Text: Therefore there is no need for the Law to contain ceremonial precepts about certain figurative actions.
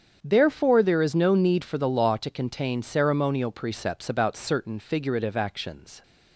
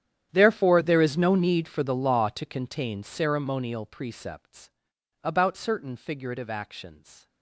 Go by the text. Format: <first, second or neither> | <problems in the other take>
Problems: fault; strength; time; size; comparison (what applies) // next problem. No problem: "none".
first | gets quieter; strong; throughout; 20 dB // starts louder than the rest; strong; until 1.3 s; 10 dB; strong in the first // pauses between "precepts" and "about"; noticeable; at 4.6 s; 0.54 s long